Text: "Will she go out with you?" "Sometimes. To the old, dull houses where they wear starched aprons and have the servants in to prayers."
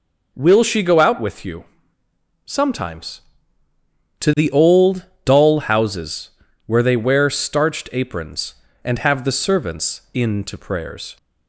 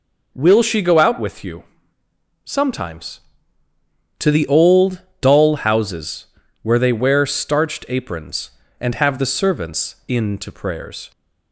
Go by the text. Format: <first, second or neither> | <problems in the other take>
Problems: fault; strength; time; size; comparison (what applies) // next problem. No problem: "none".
neither | pauses between "houses" and "where"; the same in both